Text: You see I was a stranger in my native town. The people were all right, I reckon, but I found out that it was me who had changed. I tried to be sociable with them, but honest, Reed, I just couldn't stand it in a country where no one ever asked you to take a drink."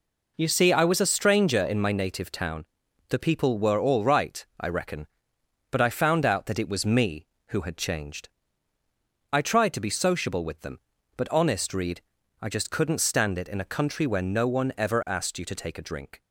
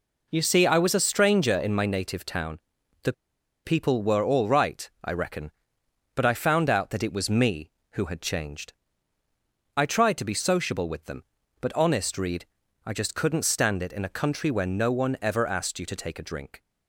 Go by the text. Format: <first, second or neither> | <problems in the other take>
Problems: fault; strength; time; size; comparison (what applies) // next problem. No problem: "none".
first | pauses between "The" and "people"; noticeable; at 3.1 s; 0.53 s long